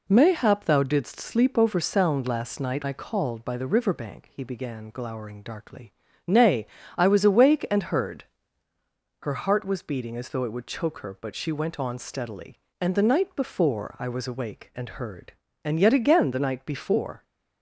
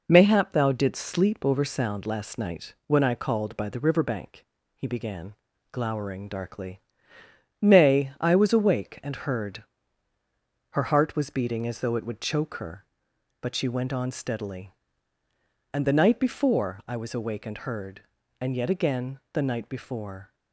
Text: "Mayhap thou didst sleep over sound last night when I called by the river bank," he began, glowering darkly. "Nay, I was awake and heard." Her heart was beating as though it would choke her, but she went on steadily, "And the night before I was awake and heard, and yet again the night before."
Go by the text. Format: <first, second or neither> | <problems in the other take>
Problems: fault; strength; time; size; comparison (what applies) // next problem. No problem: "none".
second | skips "when"; at 2.8 s